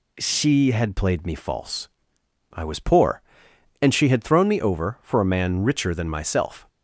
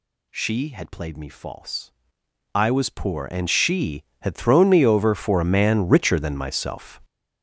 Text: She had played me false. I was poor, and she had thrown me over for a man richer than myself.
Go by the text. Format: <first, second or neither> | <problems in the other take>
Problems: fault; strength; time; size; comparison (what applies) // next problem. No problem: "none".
first | gets louder; strong; throughout; 10 dB